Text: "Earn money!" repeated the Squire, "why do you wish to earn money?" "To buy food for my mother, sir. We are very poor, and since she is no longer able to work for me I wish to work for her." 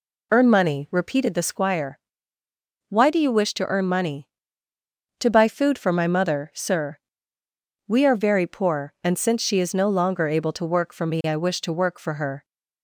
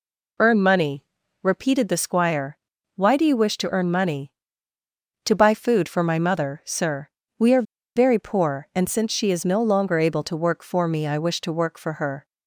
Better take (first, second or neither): first